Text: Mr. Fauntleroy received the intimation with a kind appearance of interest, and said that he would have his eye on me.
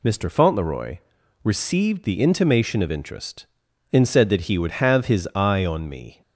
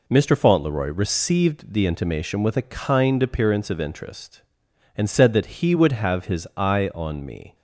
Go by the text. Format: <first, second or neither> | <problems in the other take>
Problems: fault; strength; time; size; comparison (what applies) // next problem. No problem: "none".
second | pauses between "Fauntleroy" and "received"; at 0.9 s; 0.44 s long // skips "with a kind appearance"; at 2.8 s